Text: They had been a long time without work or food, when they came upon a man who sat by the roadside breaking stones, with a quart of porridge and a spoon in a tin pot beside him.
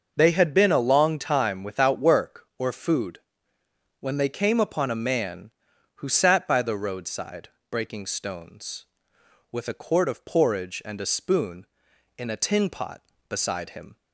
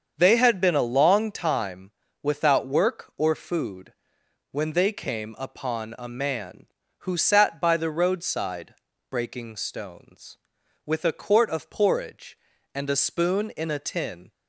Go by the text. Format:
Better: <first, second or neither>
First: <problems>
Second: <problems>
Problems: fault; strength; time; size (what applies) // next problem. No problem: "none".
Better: first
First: starts louder than the rest; until 1.1 s; 6.5 dB // pauses between "roadside" and "breaking"; slight; at 7.4 s; 0.22 s long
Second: starts louder than the rest; until 1.1 s; 7 dB // pauses between "time" and "without"; slight; at 1.9 s; 0.32 s long // pauses between "roadside" and "breaking"; at 8.7 s; 0.38 s long // stops before "pot beside him"; at 14.3 s